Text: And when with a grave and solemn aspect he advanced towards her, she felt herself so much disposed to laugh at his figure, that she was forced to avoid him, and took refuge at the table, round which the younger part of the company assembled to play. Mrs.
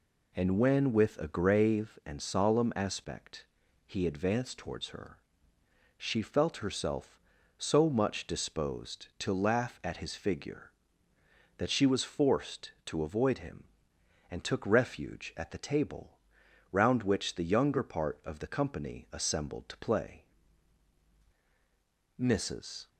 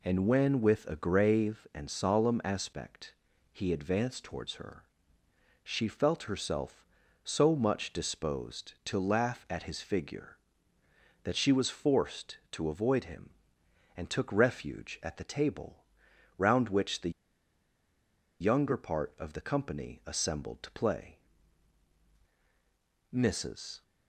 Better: first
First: pauses between "aspect" and "he"; at 3.4 s; 0.40 s long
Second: pauses between "aspect" and "he"; at 3.1 s; 0.38 s long // pauses between "the" and "younger"; strong; at 17.1 s; 1.3 s long

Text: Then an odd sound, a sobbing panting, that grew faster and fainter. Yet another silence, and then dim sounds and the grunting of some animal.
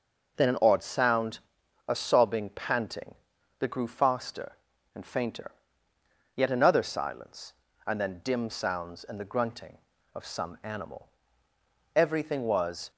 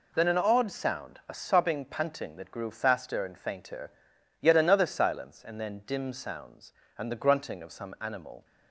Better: second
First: goes on to say "Everything was"; noticeable; from 11.9 s on; 0.96 s long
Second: none

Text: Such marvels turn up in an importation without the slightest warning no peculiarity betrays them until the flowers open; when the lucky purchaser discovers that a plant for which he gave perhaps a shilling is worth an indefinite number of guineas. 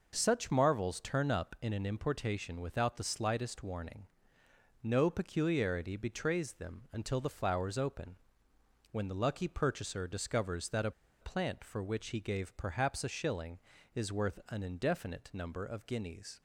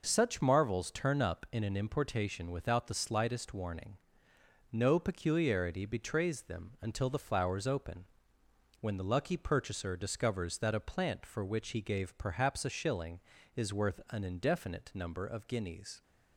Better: second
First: pauses between "warning" and "no"; noticeable; at 4.0 s; 0.74 s long // pauses between "a" and "plant"; slight; at 10.9 s; 0.29 s long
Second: pauses between "warning" and "no"; noticeable; at 3.9 s; 0.72 s long

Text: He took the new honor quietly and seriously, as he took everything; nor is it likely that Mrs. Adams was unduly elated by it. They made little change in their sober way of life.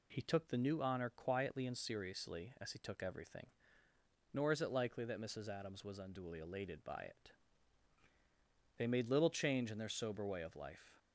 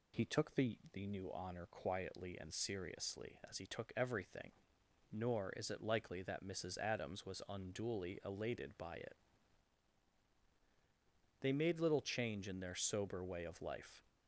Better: first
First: none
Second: says "the" twice; at 0.9 s

